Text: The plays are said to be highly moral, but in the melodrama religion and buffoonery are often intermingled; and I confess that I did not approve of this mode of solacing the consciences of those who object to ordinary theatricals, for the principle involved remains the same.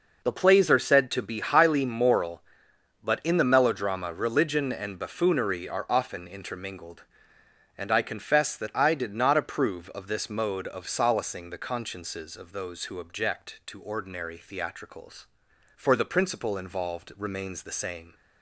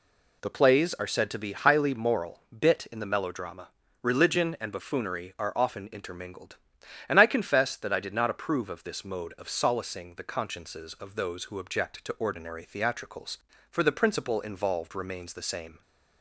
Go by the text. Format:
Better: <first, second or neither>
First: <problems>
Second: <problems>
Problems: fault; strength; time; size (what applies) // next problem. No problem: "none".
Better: first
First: none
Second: says "bit" for "but"; at 2.5 s // pauses between "melodrama" and "religion"; slight; at 3.6 s; 0.34 s long